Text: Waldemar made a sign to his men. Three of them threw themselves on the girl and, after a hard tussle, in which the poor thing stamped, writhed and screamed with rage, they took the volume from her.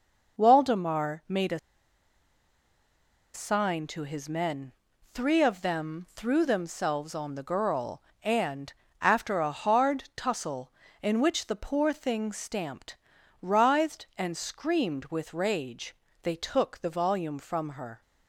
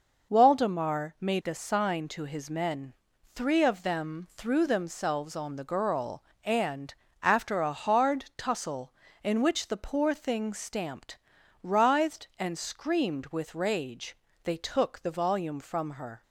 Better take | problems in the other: second | pauses between "a" and "sign"; strong; at 1.5 s; 1.7 s long

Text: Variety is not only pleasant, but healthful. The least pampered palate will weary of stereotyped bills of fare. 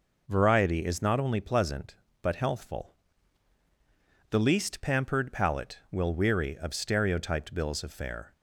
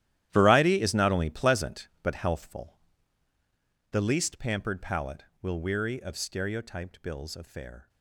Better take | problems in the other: first | gets quieter; strong; throughout; 15.5 dB

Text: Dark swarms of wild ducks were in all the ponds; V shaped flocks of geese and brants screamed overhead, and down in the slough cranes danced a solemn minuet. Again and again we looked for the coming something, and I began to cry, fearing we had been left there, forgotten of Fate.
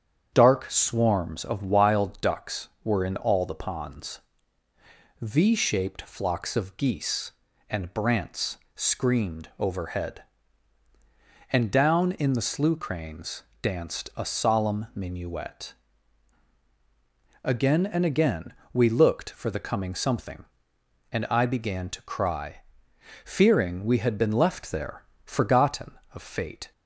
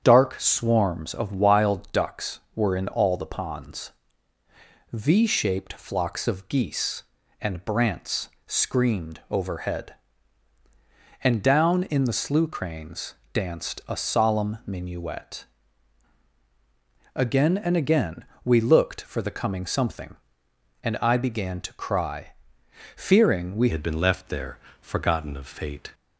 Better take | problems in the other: first | starts louder than the rest; strong; until 1.0 s; 8 dB; strong in the first // pauses between "brants" and "screamed"; slight; at 8.2 s; 0.18 s long; slight in the first // pauses between "cranes" and "danced"; slight; at 13.1 s; 0.18 s long; slight in the first // pauses between "again" and "we"; slight; at 18.2 s; 0.18 s long; slight in the first // changes voice at "had"; from 23.7 s on; 2.2 s long

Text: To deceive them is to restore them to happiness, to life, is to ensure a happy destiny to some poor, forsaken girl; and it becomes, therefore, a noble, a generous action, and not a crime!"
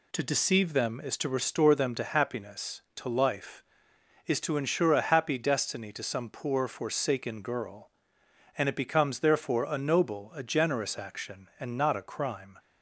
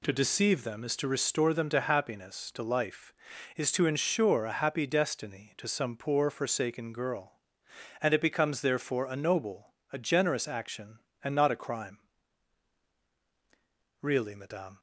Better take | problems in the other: first | goes on to say "Really madame"; noticeable; from 14.0 s on; 0.78 s long

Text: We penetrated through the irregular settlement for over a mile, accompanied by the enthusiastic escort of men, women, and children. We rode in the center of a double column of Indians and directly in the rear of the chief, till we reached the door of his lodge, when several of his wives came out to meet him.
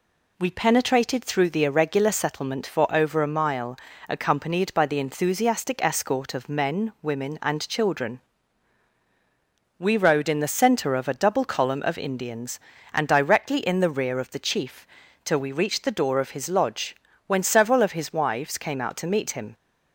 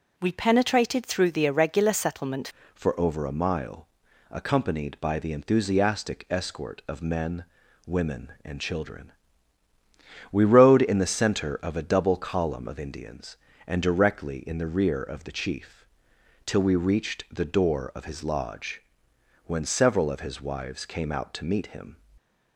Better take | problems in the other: first | changes voice at "for"; from 2.7 s on; 19.2 s long

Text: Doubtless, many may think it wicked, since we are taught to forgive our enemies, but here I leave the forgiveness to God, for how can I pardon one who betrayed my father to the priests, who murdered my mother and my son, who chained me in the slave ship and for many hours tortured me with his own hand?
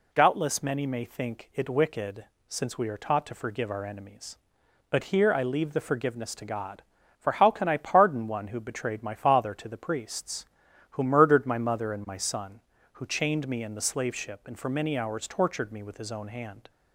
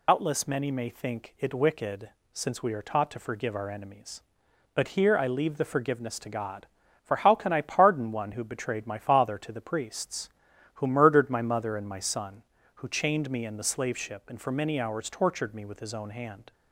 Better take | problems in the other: first | loses the start of "Doubtless"; at 0.0 s; 100 ms

